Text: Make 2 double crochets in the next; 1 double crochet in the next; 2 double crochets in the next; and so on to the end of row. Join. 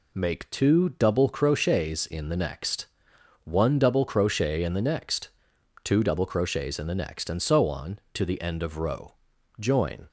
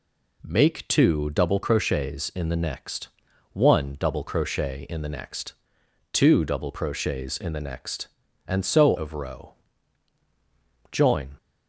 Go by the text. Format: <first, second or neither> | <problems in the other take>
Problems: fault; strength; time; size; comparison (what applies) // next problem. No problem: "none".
first | skips "on to the end"; at 8.9 s